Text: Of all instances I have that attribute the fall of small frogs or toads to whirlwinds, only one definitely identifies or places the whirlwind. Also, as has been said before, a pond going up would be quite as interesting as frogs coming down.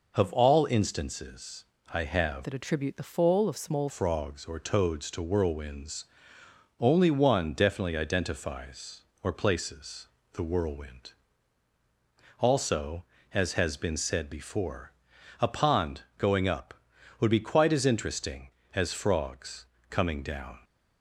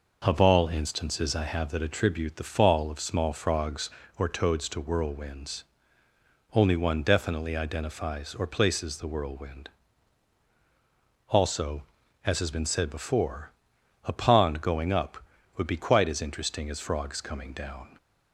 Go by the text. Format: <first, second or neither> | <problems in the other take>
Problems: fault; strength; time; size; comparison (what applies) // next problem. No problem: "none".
second | pauses between "instances" and "I"; slight; at 1.6 s; 0.28 s long // changes voice from "that" to "small"; from 2.4 to 3.8 s; 1.4 s long // pauses between "places" and "the"; slight; at 10.0 s; 0.26 s long // pauses between "pond" and "going"; slight; at 16.0 s; 0.16 s long // pauses between "frogs" and "coming"; slight; at 19.6 s; 0.24 s long